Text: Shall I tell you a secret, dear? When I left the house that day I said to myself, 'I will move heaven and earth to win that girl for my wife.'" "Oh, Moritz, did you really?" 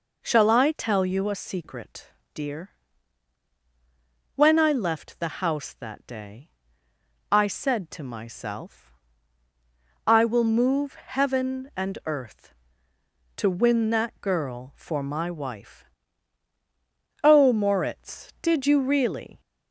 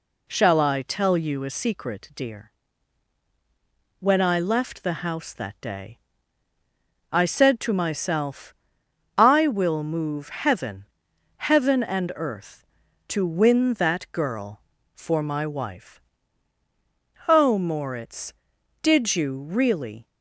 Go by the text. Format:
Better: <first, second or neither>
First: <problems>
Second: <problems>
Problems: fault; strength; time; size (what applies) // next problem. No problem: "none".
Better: first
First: pauses between "day" and "I"; noticeable; at 6.4 s; 0.84 s long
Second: pauses between "day" and "I"; at 5.9 s; 1.1 s long // says "heaven" twice; at 11.3 s